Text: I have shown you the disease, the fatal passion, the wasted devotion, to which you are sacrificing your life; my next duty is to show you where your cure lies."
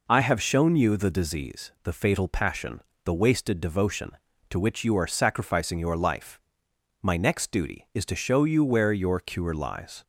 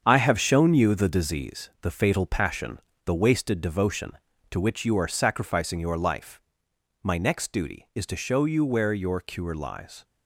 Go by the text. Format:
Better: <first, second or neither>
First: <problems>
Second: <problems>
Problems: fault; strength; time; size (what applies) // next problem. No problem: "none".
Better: first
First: none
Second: gets quieter; strong; throughout; 8.5 dB